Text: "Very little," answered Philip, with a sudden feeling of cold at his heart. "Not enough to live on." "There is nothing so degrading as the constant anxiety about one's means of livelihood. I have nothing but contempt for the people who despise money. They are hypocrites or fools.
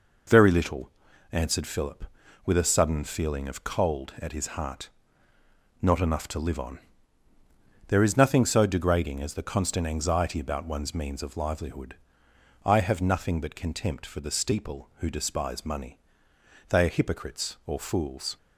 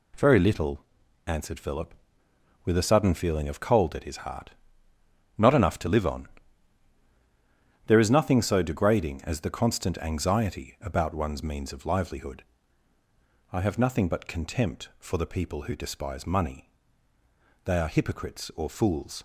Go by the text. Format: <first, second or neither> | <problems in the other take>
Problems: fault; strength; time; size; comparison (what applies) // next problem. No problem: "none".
second | says "steeple" for "people"; at 14.3 s